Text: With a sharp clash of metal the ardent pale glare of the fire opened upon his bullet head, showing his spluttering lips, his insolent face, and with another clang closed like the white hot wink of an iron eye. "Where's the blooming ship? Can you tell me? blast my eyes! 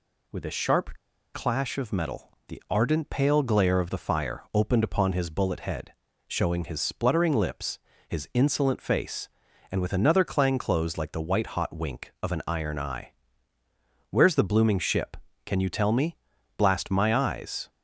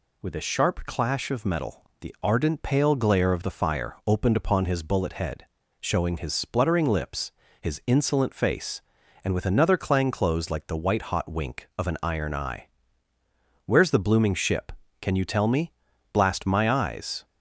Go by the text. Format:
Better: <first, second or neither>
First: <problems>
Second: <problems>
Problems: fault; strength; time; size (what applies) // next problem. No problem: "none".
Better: second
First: pauses between "sharp" and "clash"; at 0.9 s; 0.39 s long // pauses between "metal" and "the"; slight; at 2.3 s; 0.16 s long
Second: pauses between "metal" and "the"; slight; at 1.8 s; 0.16 s long